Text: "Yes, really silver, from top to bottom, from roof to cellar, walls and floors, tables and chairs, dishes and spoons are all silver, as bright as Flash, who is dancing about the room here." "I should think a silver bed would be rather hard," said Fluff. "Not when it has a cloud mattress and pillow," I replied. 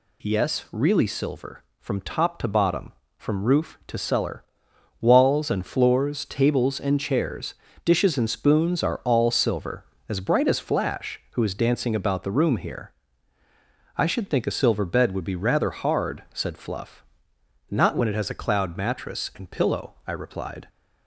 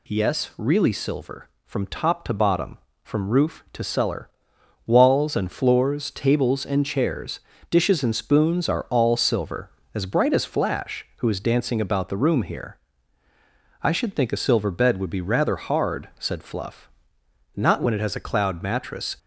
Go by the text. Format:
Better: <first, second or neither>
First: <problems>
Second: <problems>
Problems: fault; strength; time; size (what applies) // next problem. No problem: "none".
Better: first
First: none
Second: stops before "and pillow I replied"; at 19.1 s